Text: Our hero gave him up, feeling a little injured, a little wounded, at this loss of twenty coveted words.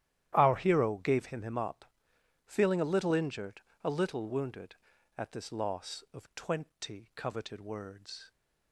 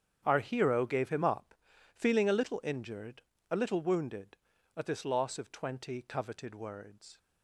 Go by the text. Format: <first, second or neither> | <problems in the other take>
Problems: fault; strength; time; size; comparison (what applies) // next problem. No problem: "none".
second | starts louder than the rest; strong; until 1.3 s; 12 dB; strong in the second // says "him" twice; at 1.4 s